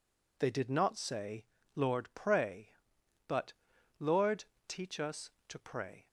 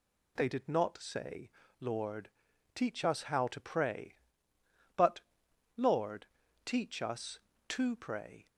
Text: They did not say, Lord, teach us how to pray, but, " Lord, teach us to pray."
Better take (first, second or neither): second